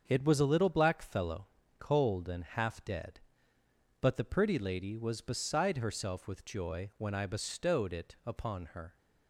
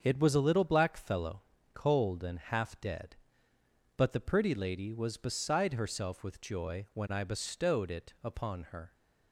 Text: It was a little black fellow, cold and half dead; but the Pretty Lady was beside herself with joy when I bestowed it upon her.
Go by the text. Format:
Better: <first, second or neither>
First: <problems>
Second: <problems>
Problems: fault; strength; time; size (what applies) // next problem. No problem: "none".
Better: neither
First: starts louder than the rest; until 1.0 s; 7 dB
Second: starts louder than the rest; until 1.0 s; 7 dB